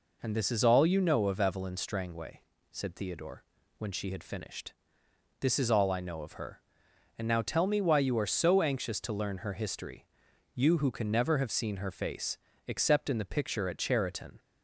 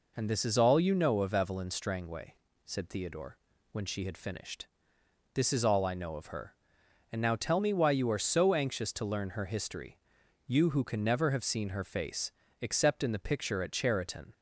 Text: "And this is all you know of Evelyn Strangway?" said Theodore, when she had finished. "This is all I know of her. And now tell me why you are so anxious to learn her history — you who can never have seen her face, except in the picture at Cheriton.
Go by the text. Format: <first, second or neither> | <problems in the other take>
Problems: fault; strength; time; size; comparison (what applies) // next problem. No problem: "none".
neither | none